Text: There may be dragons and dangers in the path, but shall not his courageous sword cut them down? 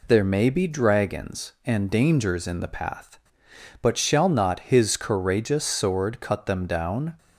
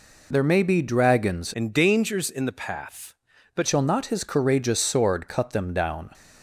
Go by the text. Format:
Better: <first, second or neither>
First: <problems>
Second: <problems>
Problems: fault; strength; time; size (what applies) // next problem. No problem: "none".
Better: first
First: none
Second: changes voice from "and" to "but"; from 1.5 to 3.6 s; 2.1 s long